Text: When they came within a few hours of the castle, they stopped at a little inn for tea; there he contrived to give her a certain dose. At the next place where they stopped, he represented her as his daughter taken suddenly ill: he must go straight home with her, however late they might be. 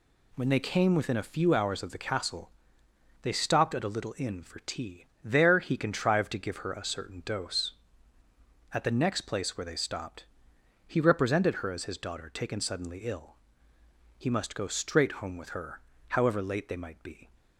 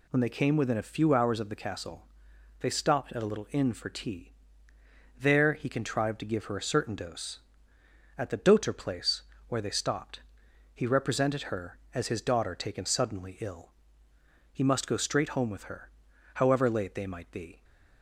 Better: first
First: none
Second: says "doter" for "next"; at 8.3 s // pauses between "place" and "where"; slight; at 9.2 s; 0.26 s long

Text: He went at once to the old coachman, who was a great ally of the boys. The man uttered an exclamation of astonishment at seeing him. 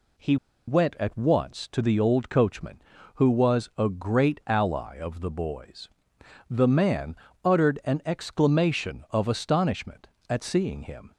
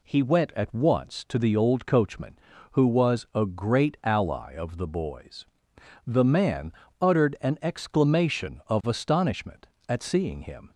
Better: second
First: pauses between "He" and "went"; slight; at 0.3 s; 0.32 s long // pauses between "man" and "uttered"; slight; at 7.1 s; 0.26 s long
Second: pauses between "man" and "uttered"; slight; at 6.7 s; 0.26 s long

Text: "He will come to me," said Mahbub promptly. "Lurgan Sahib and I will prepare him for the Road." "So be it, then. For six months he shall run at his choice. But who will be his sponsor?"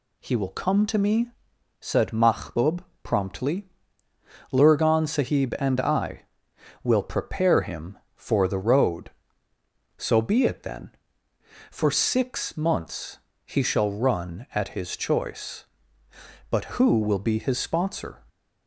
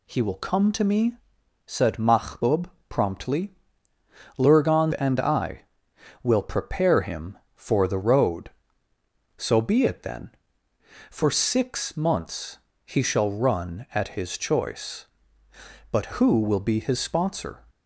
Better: first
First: pauses between "Mahbub" and "promptly"; slight; at 2.8 s; 0.20 s long // pauses between "months" and "he"; slight; at 13.1 s; 0.28 s long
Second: pauses between "Mahbub" and "promptly"; slight; at 2.7 s; 0.20 s long // skips "Sahib"; at 4.9 s // pauses between "months" and "he"; slight; at 12.5 s; 0.28 s long

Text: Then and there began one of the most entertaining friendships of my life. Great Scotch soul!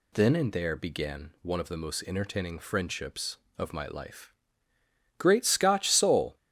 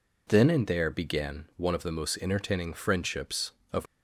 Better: first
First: none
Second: stops before "my life Great Scotch soul"; at 3.8 s

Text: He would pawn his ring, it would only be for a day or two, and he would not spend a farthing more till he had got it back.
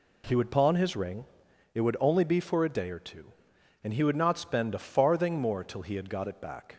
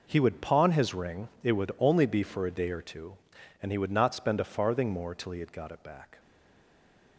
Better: first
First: none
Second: stays silent after the last word; from 6.1 s on; 1.0 s long

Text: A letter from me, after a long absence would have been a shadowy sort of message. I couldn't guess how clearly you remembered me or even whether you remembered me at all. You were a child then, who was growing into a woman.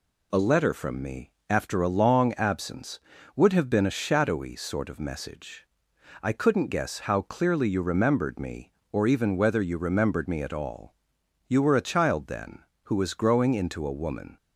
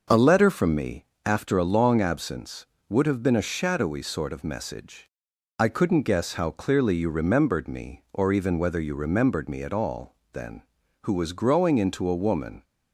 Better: first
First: none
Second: starts louder than the rest; noticeable; until 1.3 s; 6 dB // skips "You were a child"; at 10.2 s

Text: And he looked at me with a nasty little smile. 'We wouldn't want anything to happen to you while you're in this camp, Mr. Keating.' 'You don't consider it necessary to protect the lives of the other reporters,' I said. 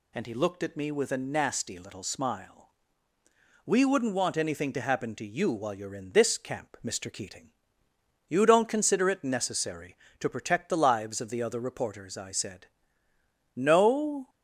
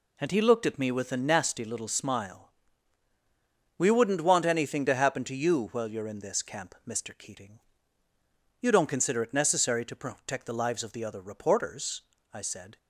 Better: second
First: goes on to say "No"; noticeable; from 13.5 s on; 0.74 s long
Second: none

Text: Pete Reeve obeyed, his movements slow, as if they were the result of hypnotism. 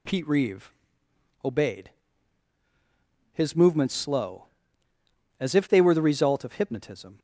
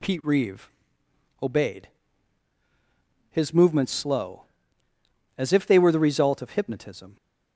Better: neither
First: pauses between "Reeve" and "obeyed"; noticeable; at 0.7 s; 0.72 s long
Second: pauses between "Reeve" and "obeyed"; noticeable; at 0.7 s; 0.72 s long

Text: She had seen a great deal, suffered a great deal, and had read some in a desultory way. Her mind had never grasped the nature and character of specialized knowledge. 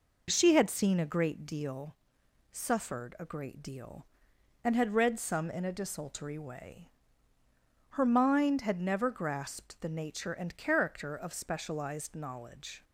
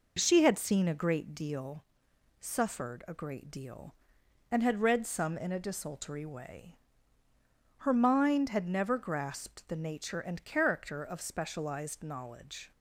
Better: neither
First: none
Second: none

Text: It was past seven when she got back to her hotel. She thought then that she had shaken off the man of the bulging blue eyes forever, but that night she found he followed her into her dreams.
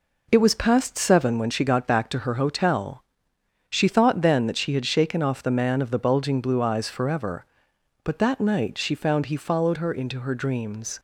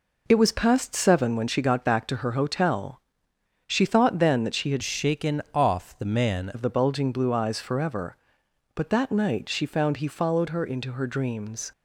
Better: first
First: none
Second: changes voice from "shaken" to "man"; from 4.8 to 6.4 s; 1.6 s long

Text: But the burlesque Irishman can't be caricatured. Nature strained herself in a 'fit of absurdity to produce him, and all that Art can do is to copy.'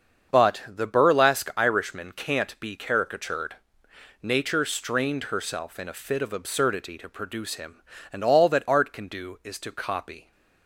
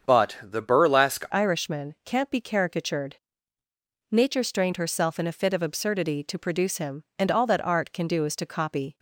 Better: first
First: starts louder than the rest; until 1.3 s; 7 dB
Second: starts louder than the rest; strong; until 1.1 s; 7.5 dB // changes voice at "Irishman"; from 1.3 s on; 7.6 s long

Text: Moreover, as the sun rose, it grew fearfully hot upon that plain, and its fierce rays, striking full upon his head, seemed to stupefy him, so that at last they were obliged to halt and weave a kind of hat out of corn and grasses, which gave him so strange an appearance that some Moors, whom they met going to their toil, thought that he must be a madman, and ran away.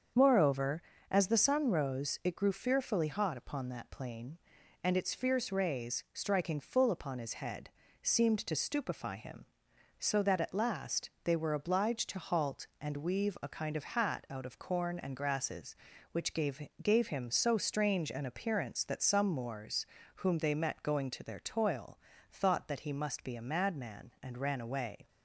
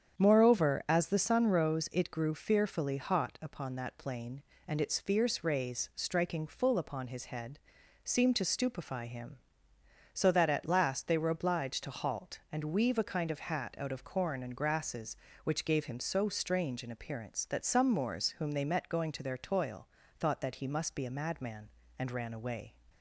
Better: second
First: starts louder than the rest; until 1.4 s; 7 dB // says "gave" twice; at 16.8 s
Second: starts louder than the rest; strong; until 1.2 s; 8.5 dB

